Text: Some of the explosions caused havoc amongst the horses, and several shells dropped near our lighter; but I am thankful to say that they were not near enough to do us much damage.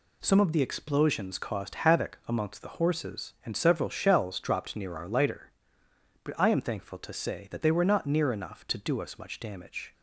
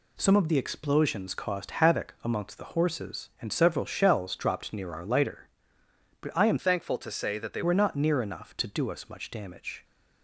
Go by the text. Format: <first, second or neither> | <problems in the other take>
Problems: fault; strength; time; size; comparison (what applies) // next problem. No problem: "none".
first | changes voice from "thankful" to "they"; from 6.5 to 7.6 s; 1.1 s long